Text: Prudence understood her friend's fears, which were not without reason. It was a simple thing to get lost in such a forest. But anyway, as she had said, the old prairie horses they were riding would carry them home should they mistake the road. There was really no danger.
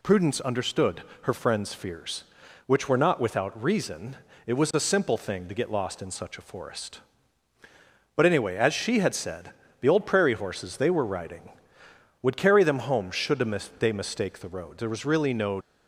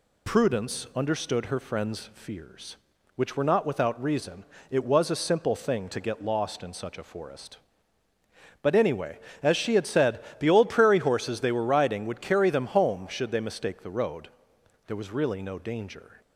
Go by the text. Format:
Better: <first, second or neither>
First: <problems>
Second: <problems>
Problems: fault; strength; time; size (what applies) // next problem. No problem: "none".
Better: second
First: pauses between "understood" and "her"; slight; at 1.0 s; 0.20 s long // pauses between "should" and "they"; at 13.3 s; 0.42 s long // stops before "danger"; at 15.6 s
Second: none